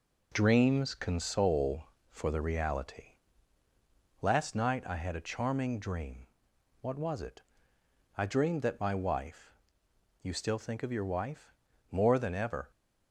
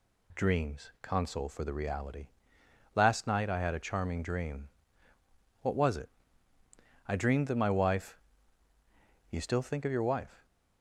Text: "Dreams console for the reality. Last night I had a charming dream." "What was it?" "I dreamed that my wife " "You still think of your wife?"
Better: second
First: goes on to say "More than ever"; noticeable; from 11.9 s on; 0.80 s long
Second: none

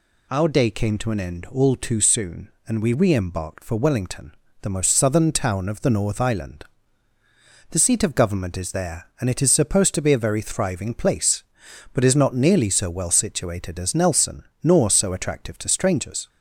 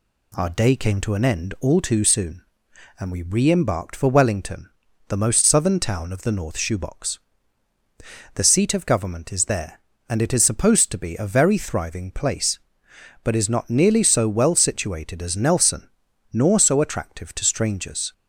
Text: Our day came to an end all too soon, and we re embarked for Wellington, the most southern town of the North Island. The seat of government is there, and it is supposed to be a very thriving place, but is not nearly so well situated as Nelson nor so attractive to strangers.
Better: first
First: pauses between "Nelson" and "nor"; slight; at 14.4 s; 0.20 s long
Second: says "Shoebox" for "Island"; at 6.5 s // pauses between "Nelson" and "nor"; noticeable; at 15.8 s; 0.46 s long

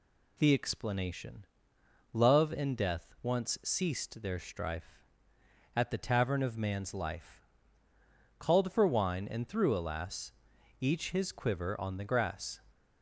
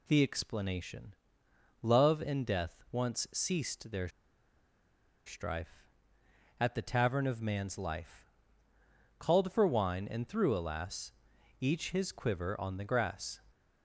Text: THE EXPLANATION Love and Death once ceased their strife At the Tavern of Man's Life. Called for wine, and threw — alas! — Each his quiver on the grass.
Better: first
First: pauses between "EXPLANATION" and "Love"; noticeable; at 1.4 s; 0.68 s long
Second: pauses between "EXPLANATION" and "Love"; noticeable; at 1.1 s; 0.68 s long // pauses between "their" and "strife"; at 4.0 s; 1.1 s long

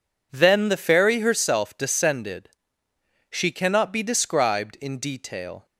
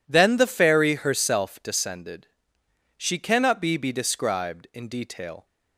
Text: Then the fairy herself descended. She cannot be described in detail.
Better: first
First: none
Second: says "be" twice; at 3.7 s

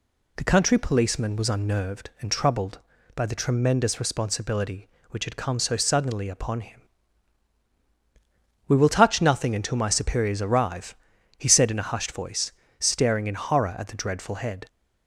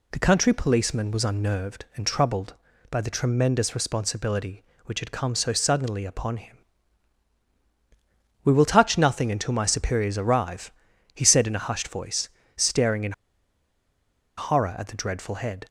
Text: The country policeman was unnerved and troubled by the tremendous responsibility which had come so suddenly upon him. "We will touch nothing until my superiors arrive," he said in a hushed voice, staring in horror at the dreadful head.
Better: first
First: none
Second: pauses between "in" and "horror"; strong; at 13.1 s; 1.2 s long

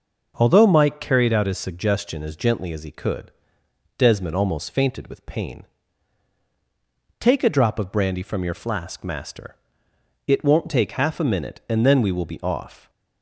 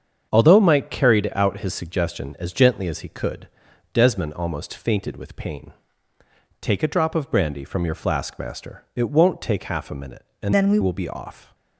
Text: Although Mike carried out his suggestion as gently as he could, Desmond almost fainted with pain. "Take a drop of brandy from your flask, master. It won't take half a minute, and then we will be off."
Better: first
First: none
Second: starts louder than the rest; strong; until 1.3 s; 7.5 dB // changes voice from "then" to "we"; from 10.5 to 10.7 s; 0.2 s long

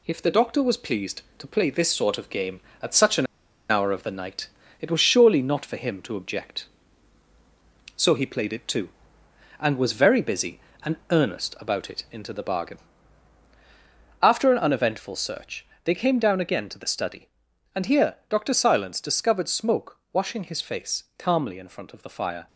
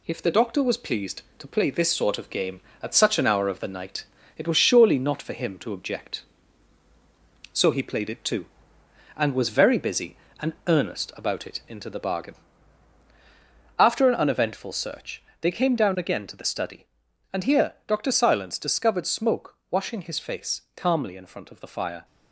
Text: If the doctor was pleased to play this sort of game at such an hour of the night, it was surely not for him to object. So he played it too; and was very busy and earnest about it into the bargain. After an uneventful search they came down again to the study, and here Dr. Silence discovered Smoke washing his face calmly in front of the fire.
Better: second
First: pauses between "an" and "hour"; at 3.2 s; 0.44 s long // pauses between "and" and "earnest"; slight; at 10.9 s; 0.16 s long // pauses between "search" and "they"; slight; at 15.6 s; 0.18 s long // pauses between "Smoke" and "washing"; slight; at 19.9 s; 0.16 s long // pauses between "face" and "calmly"; slight; at 21.0 s; 0.16 s long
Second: pauses between "and" and "earnest"; slight; at 10.5 s; 0.16 s long // pauses between "search" and "they"; slight; at 15.2 s; 0.18 s long // pauses between "Smoke" and "washing"; slight; at 19.5 s; 0.16 s long // pauses between "face" and "calmly"; slight; at 20.6 s; 0.16 s long

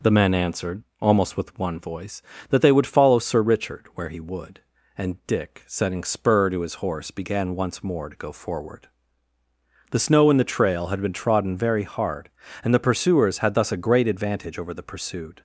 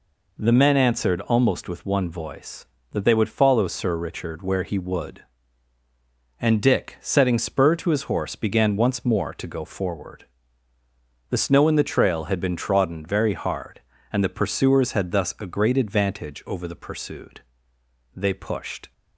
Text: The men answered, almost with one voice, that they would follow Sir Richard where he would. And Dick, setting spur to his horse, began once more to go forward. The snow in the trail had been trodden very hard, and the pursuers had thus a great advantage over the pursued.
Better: first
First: none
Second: goes on to say "They pushed"; noticeable; from 18.1 s on; 0.78 s long

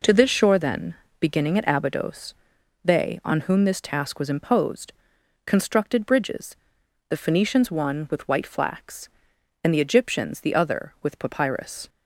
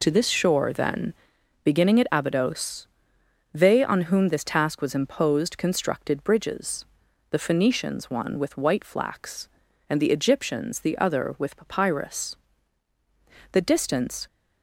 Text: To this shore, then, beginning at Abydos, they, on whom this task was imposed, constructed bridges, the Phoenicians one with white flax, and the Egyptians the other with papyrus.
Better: first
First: none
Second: goes on to say "The distance"; noticeable; from 13.5 s on; 0.74 s long

